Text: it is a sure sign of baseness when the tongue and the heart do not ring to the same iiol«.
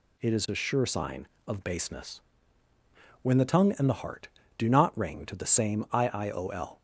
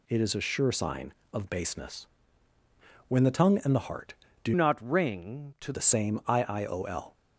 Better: first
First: pauses between "baseness" and "when"; at 2.1 s; 1.0 s long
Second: pauses between "baseness" and "when"; at 2.0 s; 1.0 s long // changes voice from "not" to "to"; from 4.5 to 5.7 s; 1.2 s long

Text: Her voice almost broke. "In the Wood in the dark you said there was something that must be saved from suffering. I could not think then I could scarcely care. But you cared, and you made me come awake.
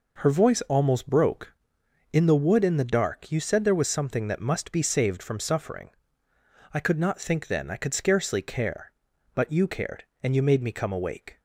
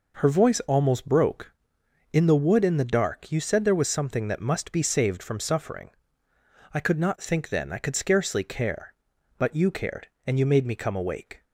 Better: neither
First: none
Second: none

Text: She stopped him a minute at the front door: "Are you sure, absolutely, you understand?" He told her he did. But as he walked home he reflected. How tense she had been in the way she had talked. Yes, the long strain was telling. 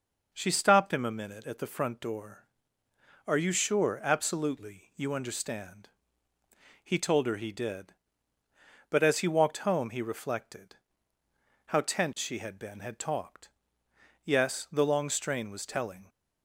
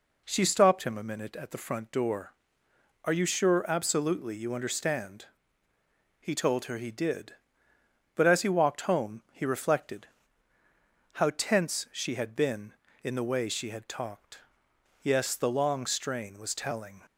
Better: second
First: skips "in the way she"; at 12.7 s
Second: none

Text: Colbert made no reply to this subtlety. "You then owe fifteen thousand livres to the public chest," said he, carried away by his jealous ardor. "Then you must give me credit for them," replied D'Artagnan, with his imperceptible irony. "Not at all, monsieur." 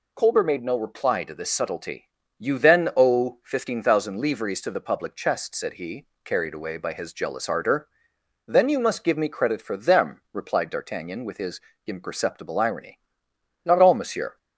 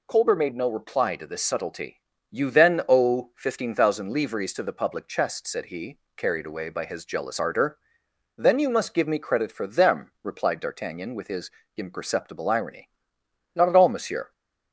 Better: second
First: pauses between "his" and "imperceptible"; slight; at 11.6 s; 0.24 s long // skips "at"; at 13.7 s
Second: pauses between "his" and "imperceptible"; slight; at 11.5 s; 0.24 s long

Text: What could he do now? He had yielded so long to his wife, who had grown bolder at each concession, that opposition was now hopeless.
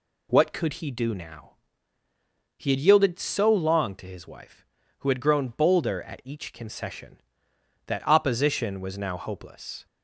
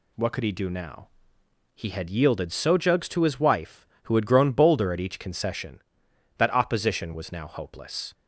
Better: first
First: none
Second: says "jugs" for "long"; at 2.7 s

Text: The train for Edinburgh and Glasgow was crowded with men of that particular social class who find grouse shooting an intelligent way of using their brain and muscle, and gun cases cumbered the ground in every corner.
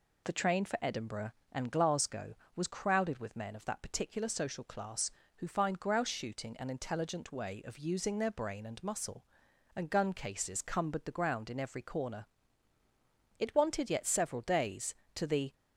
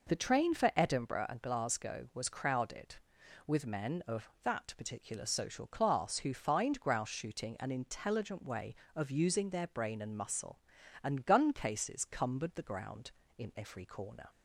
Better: second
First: goes on to say "It wanted yet several days to the"; strong; from 13.3 s on; 2.1 s long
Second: none

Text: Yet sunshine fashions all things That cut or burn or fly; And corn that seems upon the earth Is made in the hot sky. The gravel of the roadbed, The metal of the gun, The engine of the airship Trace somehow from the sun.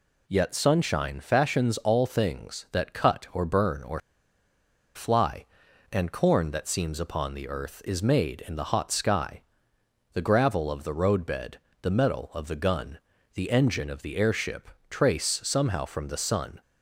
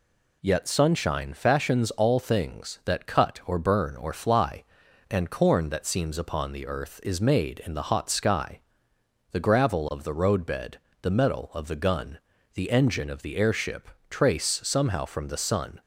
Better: second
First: pauses between "or" and "fly"; noticeable; at 4.0 s; 0.95 s long // pauses between "airship" and "Trace"; slight; at 14.6 s; 0.20 s long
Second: pauses between "airship" and "Trace"; slight; at 13.8 s; 0.20 s long

